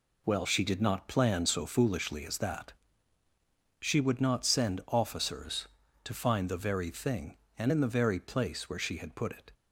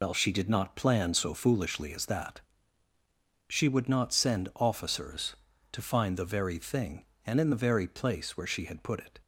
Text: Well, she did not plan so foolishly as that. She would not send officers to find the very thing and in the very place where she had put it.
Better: first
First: none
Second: loses the start of "Well"; at 0.0 s; 85 ms

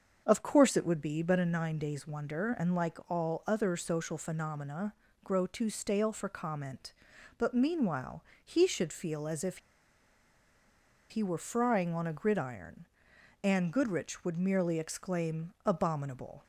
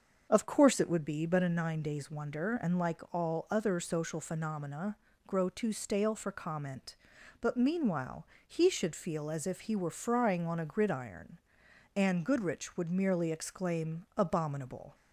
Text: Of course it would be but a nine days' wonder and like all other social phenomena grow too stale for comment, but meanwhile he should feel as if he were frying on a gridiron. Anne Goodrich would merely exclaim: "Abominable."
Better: second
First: starts louder than the rest; until 1.2 s; 6.5 dB // pauses between "phenomena" and "grow"; slight; at 4.9 s; 0.32 s long // pauses between "meanwhile" and "he"; slight; at 8.2 s; 0.22 s long // pauses between "if" and "he"; strong; at 9.5 s; 1.5 s long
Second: starts louder than the rest; until 1.3 s; 6.5 dB // pauses between "phenomena" and "grow"; slight; at 4.9 s; 0.32 s long // pauses between "meanwhile" and "he"; slight; at 8.2 s; 0.22 s long

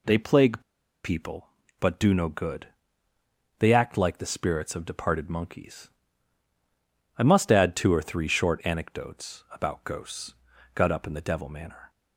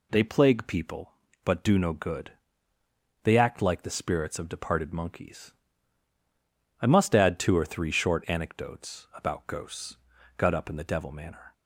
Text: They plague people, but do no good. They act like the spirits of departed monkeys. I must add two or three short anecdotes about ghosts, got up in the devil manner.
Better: second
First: pauses between "plague" and "people"; at 0.6 s; 0.43 s long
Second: none

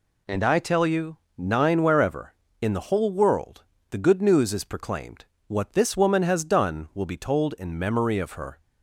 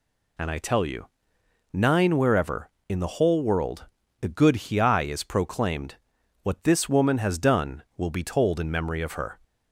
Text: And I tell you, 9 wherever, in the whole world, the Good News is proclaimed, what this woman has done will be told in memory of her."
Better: first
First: none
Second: says "Hiai" for "News"; at 4.6 s

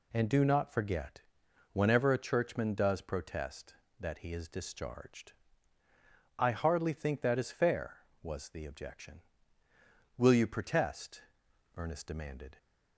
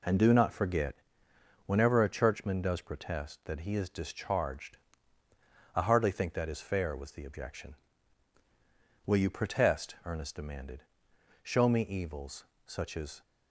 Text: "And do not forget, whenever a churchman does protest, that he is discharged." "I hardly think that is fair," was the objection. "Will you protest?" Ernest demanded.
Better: first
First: none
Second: goes on to say "Show me evils such as"; strong; from 11.4 s on; 1.8 s long

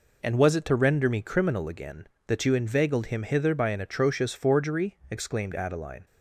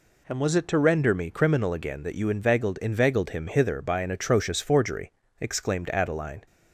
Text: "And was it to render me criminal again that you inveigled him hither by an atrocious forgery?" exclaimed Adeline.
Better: first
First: none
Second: says "inveigled" twice; at 2.7 s

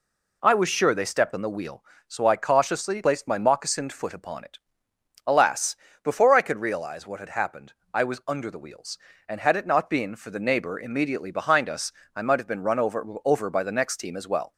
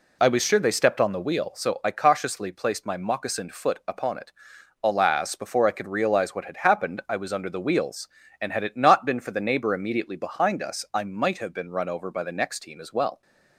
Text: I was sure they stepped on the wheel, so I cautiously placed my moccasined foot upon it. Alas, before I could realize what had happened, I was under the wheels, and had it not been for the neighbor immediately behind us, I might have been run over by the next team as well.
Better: second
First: says "over" twice; at 13.2 s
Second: none

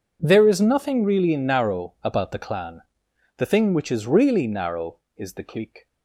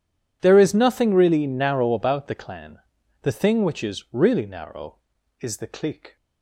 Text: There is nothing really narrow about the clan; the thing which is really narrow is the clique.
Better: neither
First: none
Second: none

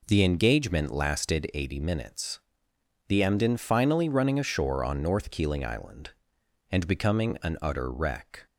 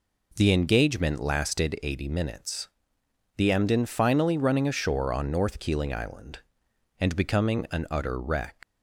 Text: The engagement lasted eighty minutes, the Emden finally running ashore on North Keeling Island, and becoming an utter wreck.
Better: first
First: none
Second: leaves "wreck" unfinished; at 8.6 s; 115 ms

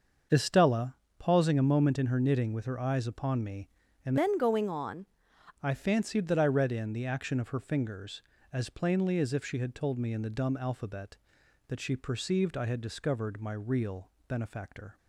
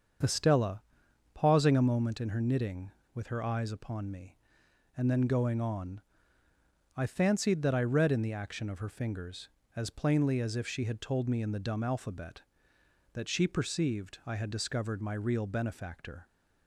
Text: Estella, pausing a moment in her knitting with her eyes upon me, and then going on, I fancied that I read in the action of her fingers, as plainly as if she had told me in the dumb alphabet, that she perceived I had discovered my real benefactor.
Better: second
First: starts louder than the rest; until 1.5 s; 6.5 dB // changes voice from "then" to "on"; from 4.1 to 5.0 s; 0.9 s long // pauses between "real" and "benefactor"; slight; at 14.0 s; 0.18 s long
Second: starts louder than the rest; until 1.7 s; 7 dB

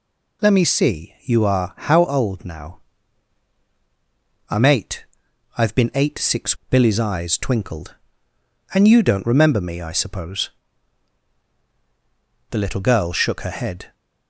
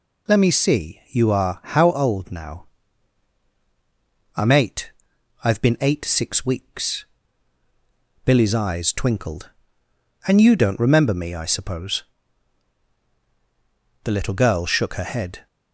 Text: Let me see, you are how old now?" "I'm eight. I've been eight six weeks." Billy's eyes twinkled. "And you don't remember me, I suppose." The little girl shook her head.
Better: second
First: skips "weeks"; at 6.6 s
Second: none

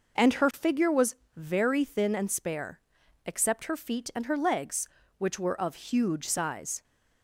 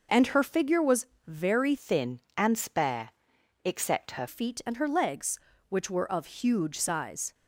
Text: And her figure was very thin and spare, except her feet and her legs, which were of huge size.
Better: first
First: pauses between "was" and "very"; slight; at 1.1 s; 0.20 s long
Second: pauses between "was" and "very"; slight; at 1.0 s; 0.20 s long // changes voice from "thin" to "her"; from 1.7 to 4.2 s; 2.5 s long

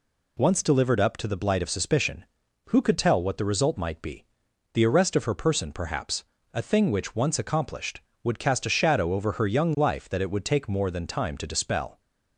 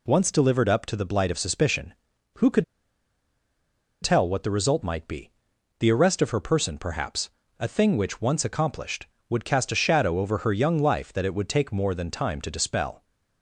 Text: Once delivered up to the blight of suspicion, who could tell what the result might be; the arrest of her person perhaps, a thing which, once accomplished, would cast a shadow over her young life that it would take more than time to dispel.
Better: first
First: none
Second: pauses between "could" and "tell"; strong; at 2.6 s; 1.3 s long

